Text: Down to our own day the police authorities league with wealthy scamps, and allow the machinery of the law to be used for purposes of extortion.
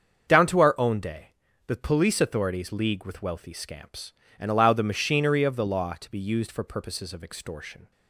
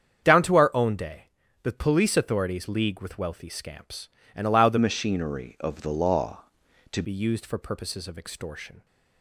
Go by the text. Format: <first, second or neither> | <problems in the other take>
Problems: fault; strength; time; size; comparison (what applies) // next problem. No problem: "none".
first | starts louder than the rest; strong; until 1.6 s; 8 dB; also in the first // pauses between "day" and "the"; at 1.2 s; 0.38 s long; also in the first // changes voice from "machinery" to "to"; from 4.7 to 7.0 s; 2.3 s long